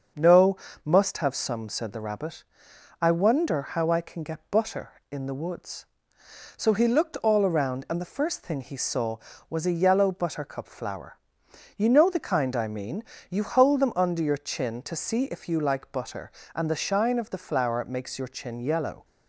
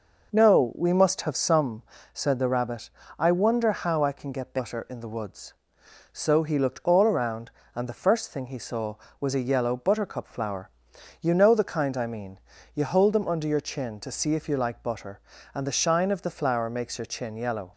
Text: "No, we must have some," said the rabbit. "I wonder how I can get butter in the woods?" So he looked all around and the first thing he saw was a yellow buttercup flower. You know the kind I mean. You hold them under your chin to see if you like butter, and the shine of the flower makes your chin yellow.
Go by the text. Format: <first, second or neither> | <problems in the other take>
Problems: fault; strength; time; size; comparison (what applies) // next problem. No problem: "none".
second | starts louder than the rest; until 1.4 s; 6.5 dB // skips "we"; at 0.6 s